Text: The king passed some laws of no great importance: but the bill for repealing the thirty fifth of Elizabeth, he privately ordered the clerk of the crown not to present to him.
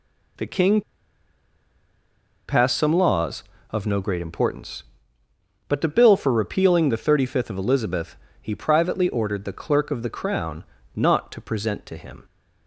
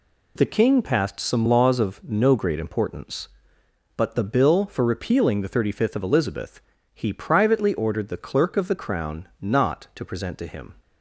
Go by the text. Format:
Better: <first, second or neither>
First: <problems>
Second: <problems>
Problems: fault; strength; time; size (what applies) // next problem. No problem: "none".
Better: second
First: pauses between "king" and "passed"; strong; at 0.8 s; 1.6 s long // pauses between "crown" and "not"; slight; at 10.6 s; 0.32 s long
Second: none